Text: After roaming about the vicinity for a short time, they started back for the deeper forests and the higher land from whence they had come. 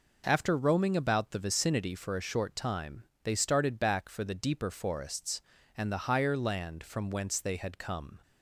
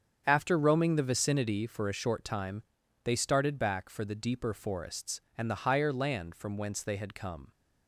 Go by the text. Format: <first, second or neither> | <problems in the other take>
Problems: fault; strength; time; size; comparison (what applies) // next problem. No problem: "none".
first | starts louder than the rest; strong; until 1.2 s; 7.5 dB // skips "about"; at 0.9 s